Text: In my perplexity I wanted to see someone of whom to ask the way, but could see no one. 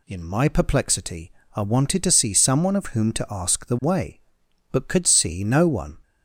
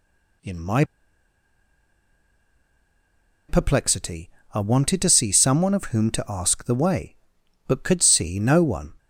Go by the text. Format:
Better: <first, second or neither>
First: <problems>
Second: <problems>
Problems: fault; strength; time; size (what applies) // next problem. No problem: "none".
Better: first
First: pauses between "perplexity" and "I"; slight; at 1.3 s; 0.24 s long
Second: pauses between "my" and "perplexity"; strong; at 0.8 s; 2.6 s long // pauses between "perplexity" and "I"; slight; at 4.2 s; 0.24 s long